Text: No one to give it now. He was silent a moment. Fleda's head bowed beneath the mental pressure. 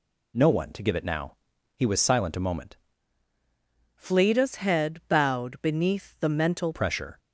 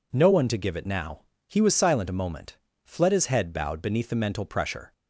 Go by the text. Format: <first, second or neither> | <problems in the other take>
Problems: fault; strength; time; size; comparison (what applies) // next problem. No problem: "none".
second | changes voice from "Fleda's" to "mental"; from 3.9 to 6.7 s; 2.8 s long